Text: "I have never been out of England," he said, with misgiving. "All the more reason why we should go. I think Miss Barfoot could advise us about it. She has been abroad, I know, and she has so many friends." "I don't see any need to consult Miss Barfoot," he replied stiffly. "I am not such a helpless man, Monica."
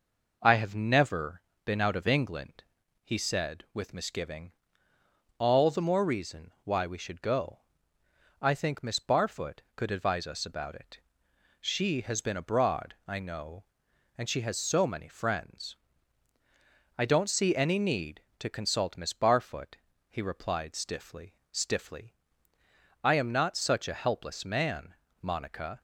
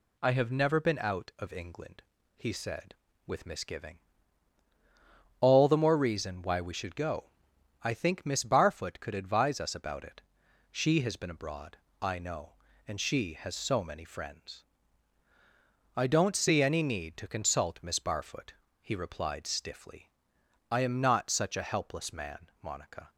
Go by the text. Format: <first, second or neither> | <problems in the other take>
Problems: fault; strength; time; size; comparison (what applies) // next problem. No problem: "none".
second | pauses between "never" and "been"; slight; at 1.4 s; 0.24 s long // says "stiffly" twice; at 21.5 s